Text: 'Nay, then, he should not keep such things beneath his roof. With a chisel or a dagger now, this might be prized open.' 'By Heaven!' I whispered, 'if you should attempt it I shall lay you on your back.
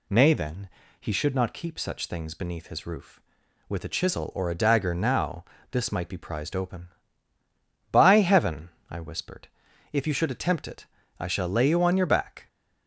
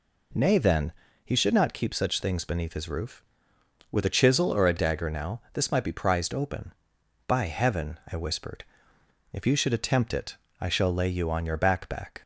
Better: first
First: pauses between "it" and "I"; slight; at 10.8 s; 0.34 s long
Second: pauses between "it" and "I"; slight; at 10.3 s; 0.24 s long // says "back" twice; at 11.8 s

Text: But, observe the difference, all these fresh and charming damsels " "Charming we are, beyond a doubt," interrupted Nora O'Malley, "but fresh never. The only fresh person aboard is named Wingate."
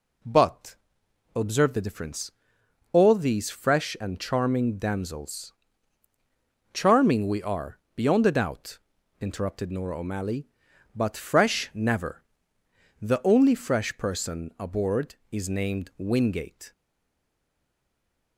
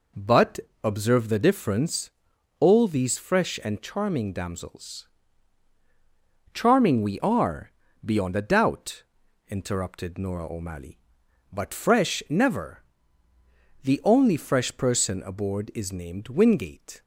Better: second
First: stays silent after the last word; noticeable; from 16.7 s on; 1.6 s long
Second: none

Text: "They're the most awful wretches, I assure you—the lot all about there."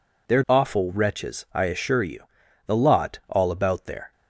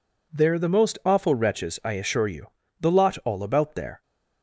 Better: second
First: skips "the most"; at 0.4 s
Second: none

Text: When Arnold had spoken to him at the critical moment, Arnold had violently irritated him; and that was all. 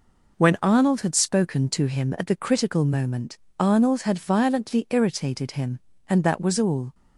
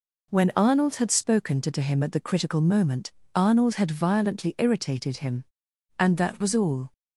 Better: first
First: none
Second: says "to" twice; at 1.7 s

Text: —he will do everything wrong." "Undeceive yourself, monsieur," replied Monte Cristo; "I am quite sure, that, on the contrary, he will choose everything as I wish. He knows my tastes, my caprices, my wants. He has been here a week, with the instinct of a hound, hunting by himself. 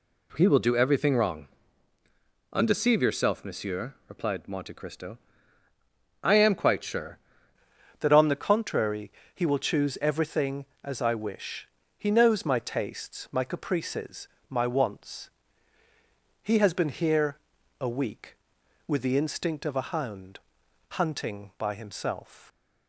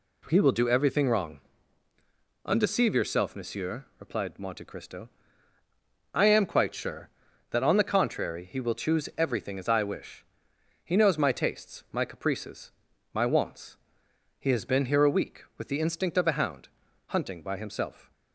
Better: second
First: changes voice at "that"; from 8.0 s on; 14.4 s long // pauses between "here" and "a"; at 17.3 s; 0.42 s long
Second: none

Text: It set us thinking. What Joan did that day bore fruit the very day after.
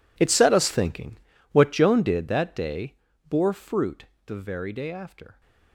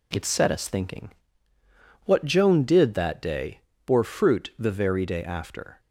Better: second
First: gets quieter; strong; throughout; 18 dB // pauses between "day" and "bore"; slight; at 2.9 s; 0.34 s long // pauses between "fruit" and "the"; slight; at 4.0 s; 0.20 s long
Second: pauses between "day" and "bore"; slight; at 3.6 s; 0.24 s long

